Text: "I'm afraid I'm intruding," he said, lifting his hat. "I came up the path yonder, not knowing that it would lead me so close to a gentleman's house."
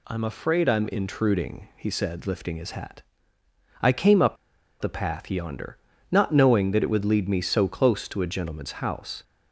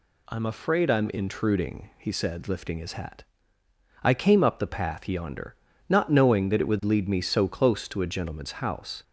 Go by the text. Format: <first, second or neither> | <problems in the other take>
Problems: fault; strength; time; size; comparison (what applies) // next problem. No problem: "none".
second | pauses between "up" and "the"; noticeable; at 4.3 s; 0.46 s long